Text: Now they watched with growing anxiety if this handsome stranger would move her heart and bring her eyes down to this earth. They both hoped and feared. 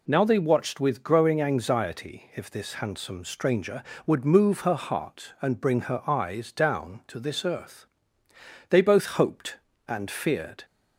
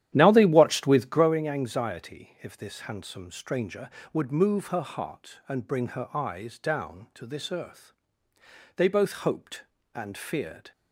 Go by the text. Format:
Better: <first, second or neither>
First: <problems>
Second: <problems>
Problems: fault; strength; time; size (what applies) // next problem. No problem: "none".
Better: first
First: none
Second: starts louder than the rest; strong; until 1.3 s; 11.5 dB